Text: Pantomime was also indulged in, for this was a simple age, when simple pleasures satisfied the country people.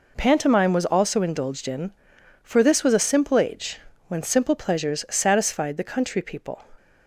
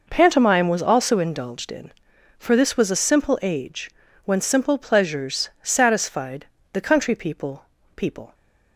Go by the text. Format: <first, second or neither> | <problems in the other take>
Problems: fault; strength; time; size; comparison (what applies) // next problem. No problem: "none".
first | pauses between "satisfied" and "the"; slight; at 6.4 s; 0.28 s long // says "people" twice; at 7.9 s